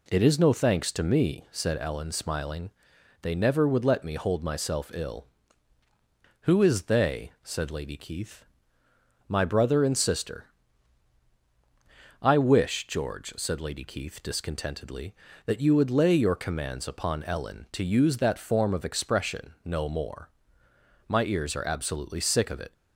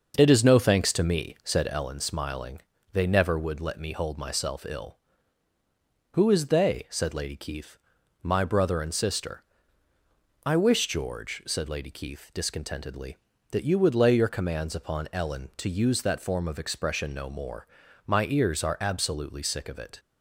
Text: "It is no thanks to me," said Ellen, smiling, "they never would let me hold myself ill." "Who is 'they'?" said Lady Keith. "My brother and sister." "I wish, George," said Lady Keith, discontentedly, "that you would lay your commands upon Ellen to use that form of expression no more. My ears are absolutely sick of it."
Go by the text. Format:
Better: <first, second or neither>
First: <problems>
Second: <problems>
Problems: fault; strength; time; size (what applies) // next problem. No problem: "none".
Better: first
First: none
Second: starts louder than the rest; until 2.0 s; 6 dB